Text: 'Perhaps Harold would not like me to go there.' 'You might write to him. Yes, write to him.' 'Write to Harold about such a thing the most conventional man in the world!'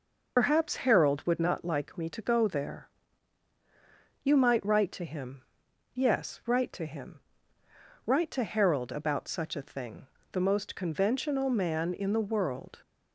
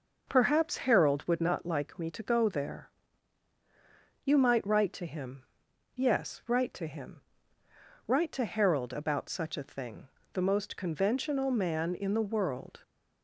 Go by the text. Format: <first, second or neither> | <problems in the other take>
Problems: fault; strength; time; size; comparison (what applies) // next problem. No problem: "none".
second | loses the start of "Perhaps"; at 0.3 s; 95 ms // pauses between "thing" and "the"; slight; at 10.0 s; 0.26 s long; slight in the second